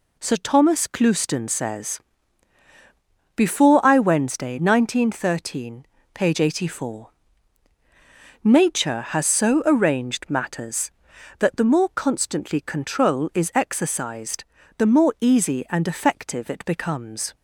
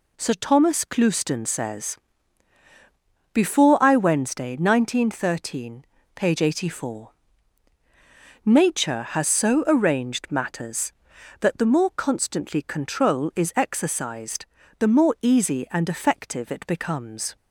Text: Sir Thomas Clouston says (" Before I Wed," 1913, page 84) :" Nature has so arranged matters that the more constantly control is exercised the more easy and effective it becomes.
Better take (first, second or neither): neither